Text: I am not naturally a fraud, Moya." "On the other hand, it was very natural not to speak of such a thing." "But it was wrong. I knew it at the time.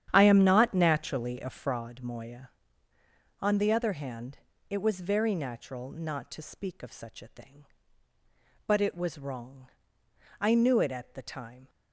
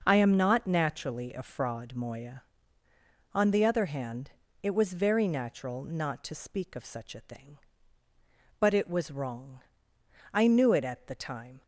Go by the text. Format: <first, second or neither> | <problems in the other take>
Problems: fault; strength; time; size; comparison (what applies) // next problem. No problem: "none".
second | starts louder than the rest; strong; until 1.8 s; 10 dB